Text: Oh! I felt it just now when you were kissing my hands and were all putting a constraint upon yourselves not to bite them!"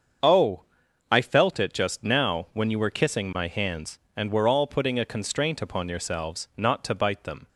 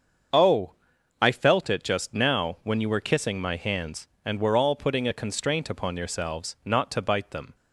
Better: neither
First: starts louder than the rest; until 1.6 s; 7 dB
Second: starts louder than the rest; until 1.7 s; 7 dB

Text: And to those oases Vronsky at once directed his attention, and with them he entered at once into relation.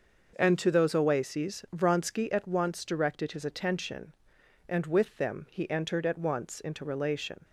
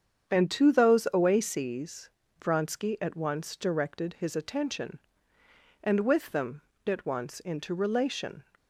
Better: first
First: starts louder than the rest; noticeable; until 1.3 s; 6 dB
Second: starts louder than the rest; strong; until 1.3 s; 8 dB // pauses between "oases" and "Vronsky"; slight; at 2.0 s; 0.32 s long // skips "he entered"; at 6.7 s

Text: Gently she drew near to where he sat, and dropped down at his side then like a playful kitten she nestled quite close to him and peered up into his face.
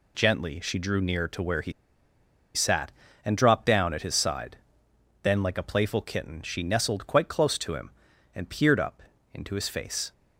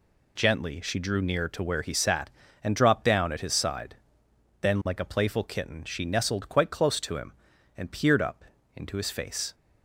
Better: second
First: pauses between "he" and "sat"; noticeable; at 1.7 s; 0.83 s long // pauses between "side" and "then"; noticeable; at 4.5 s; 0.68 s long // pauses between "up" and "into"; slight; at 9.0 s; 0.32 s long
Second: pauses between "side" and "then"; noticeable; at 3.9 s; 0.68 s long // pauses between "up" and "into"; slight; at 8.4 s; 0.32 s long

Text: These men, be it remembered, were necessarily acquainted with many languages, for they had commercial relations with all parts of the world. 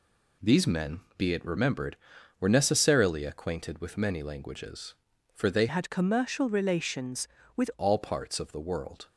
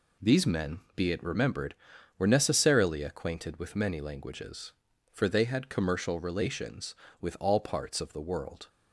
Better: second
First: changes voice from "had" to "with"; from 5.6 to 7.7 s; 2.1 s long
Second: none

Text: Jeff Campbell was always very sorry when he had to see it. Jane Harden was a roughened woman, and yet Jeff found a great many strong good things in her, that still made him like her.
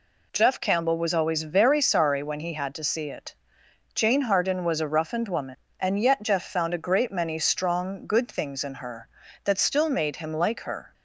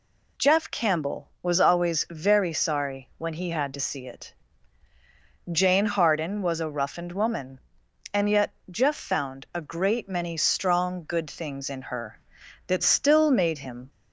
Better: first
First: none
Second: pauses between "yet" and "Jeff"; slight; at 8.4 s; 0.20 s long // stops before "like her"; at 13.8 s

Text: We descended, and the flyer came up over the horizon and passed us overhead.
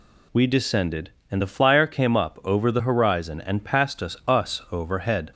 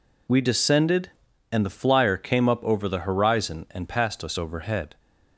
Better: second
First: says "us" twice; at 4.2 s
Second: none

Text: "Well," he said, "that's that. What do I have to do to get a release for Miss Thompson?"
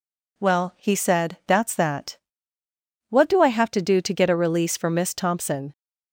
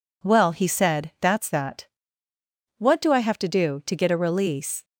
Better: first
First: none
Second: stops before "for Miss Thompson"; at 4.8 s

